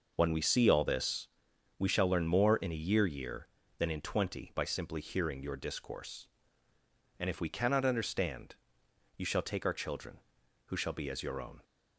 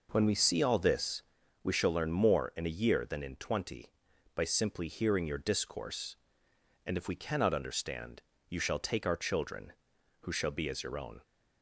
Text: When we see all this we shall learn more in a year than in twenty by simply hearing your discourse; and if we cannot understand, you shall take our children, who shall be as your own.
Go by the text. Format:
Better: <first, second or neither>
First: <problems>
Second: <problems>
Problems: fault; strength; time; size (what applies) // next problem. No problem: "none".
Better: second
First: pauses between "this" and "we"; noticeable; at 1.2 s; 0.52 s long // says "year" twice; at 3.0 s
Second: pauses between "this" and "we"; at 1.2 s; 0.40 s long